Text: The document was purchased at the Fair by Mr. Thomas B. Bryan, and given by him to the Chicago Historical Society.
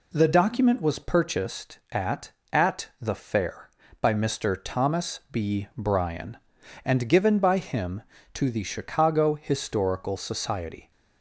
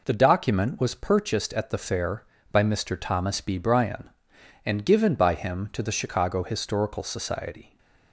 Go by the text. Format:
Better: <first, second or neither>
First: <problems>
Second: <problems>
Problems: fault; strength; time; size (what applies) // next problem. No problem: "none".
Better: second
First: says "at" twice; at 2.5 s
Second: none